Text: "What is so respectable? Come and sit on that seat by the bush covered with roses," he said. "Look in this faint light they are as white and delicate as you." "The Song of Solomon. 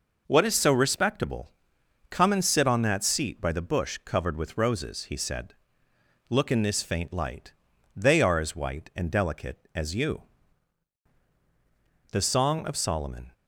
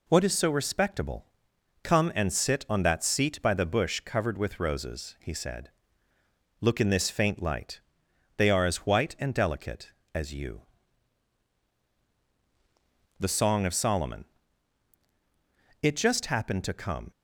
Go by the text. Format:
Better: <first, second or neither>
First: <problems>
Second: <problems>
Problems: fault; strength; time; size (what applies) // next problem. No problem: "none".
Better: first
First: pauses between "light" and "they"; at 7.5 s; 0.42 s long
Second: pauses between "light" and "they"; noticeable; at 7.8 s; 0.56 s long // goes on to say "It just happened to come"; noticeable; from 15.8 s on; 1.2 s long